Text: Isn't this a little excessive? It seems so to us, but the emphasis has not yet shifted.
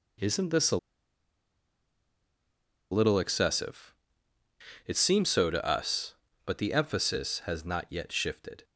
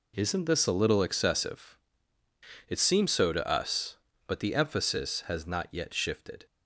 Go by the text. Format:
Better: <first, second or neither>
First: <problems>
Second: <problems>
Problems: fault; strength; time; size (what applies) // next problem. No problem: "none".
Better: second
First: pauses between "a" and "little"; strong; at 0.7 s; 2.1 s long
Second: none